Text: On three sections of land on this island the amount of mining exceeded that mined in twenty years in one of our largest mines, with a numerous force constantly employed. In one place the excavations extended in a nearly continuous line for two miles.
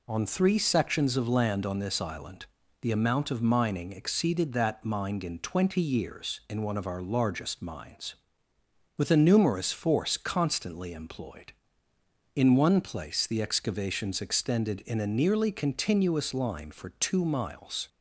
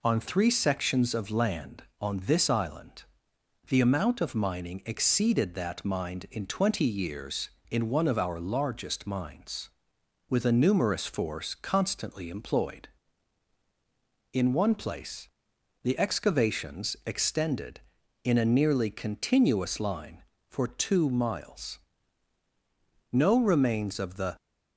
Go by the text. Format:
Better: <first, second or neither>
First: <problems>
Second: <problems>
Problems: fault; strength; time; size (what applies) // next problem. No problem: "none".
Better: first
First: pauses between "island" and "the"; slight; at 2.4 s; 0.36 s long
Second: pauses between "island" and "the"; noticeable; at 3.0 s; 0.66 s long // pauses between "place" and "the"; noticeable; at 15.2 s; 0.56 s long // goes on to say "No remains of the"; noticeable; from 23.1 s on; 1.2 s long